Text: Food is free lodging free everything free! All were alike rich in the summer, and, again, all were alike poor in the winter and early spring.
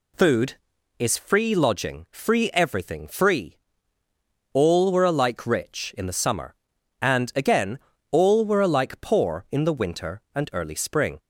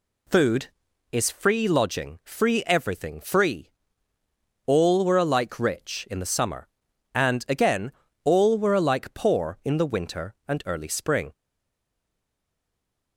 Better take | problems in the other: first | stays silent after the last word; noticeable; from 11.3 s on; 1.8 s long

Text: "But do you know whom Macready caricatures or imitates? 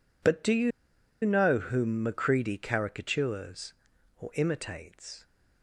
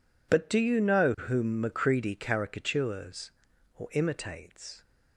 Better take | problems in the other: second | pauses between "you" and "know"; noticeable; at 0.7 s; 0.53 s long

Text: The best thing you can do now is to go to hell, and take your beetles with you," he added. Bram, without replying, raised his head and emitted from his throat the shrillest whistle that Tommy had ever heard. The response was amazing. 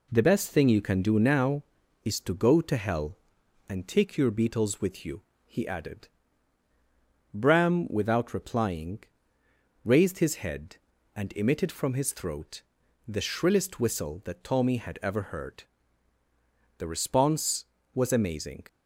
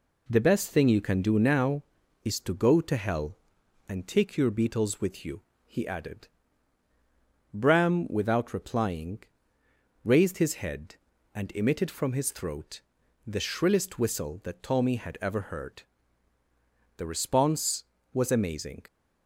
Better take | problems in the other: neither | pauses between "throat" and "the"; noticeable; the same in both

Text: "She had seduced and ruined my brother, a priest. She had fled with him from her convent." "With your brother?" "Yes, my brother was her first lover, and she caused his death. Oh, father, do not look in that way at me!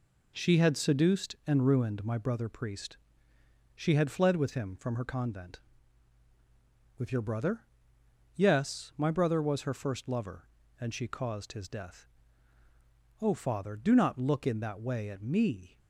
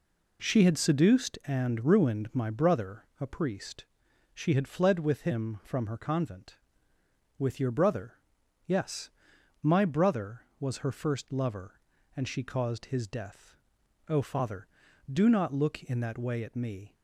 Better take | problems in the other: second | skips "a"; at 2.4 s

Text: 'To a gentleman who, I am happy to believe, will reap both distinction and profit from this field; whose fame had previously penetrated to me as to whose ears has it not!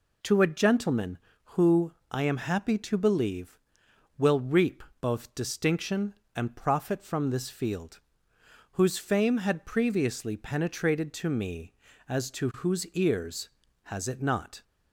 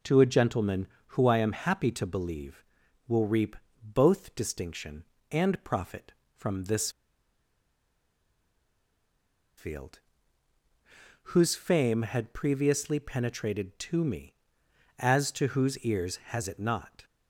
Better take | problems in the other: first | pauses between "reap" and "both"; slight; at 3.5 s; 0.28 s long; slight in the first // pauses between "this" and "field"; strong; at 6.8 s; 2.6 s long

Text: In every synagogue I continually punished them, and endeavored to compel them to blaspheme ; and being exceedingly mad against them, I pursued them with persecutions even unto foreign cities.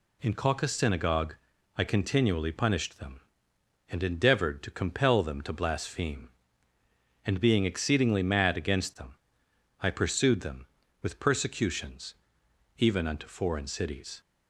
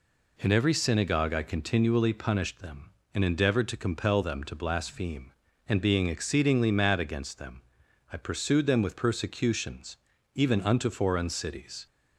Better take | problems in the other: second | says "caucus" for "every"; at 0.3 s // pauses between "synagogue" and "I"; at 1.3 s; 0.42 s long // pauses between "persecutions" and "even"; noticeable; at 12.1 s; 0.64 s long; also in the second

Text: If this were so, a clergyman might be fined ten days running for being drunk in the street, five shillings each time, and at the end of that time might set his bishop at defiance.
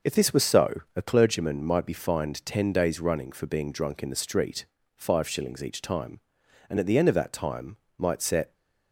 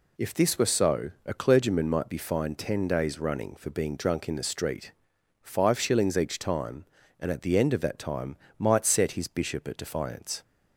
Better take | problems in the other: second | starts louder than the rest; until 1.2 s; 6.5 dB // pauses between "time" and "might"; slight; at 7.7 s; 0.24 s long; slight in the second // stops before "his bishop at defiance"; at 8.5 s

